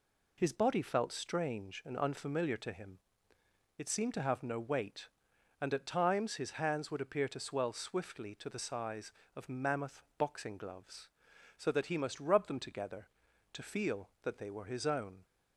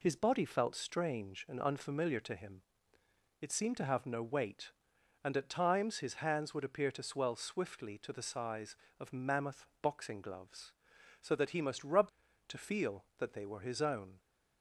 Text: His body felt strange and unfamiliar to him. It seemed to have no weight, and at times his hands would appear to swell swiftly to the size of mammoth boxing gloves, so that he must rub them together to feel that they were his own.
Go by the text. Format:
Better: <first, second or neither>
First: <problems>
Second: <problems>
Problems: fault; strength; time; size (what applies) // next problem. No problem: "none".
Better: first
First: none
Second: skips "them together"; at 12.2 s